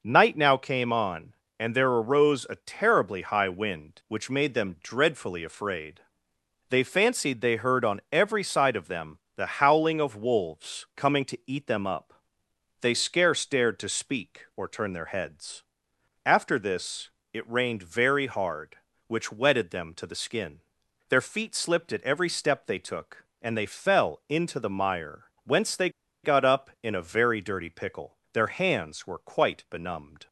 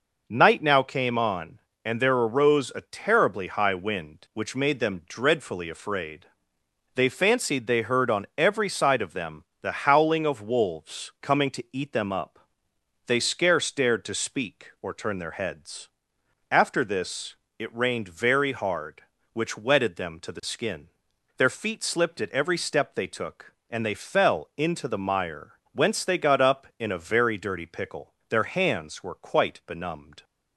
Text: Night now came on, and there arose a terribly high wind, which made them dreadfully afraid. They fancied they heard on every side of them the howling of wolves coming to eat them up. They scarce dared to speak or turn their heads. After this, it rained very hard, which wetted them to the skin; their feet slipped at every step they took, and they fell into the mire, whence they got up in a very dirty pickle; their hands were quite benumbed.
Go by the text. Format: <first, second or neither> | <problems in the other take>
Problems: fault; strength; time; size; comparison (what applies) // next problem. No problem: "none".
second | pauses between "them" and "the"; slight; at 9.1 s; 0.18 s long; slight in the second // pauses between "they" and "got"; slight; at 25.8 s; 0.34 s long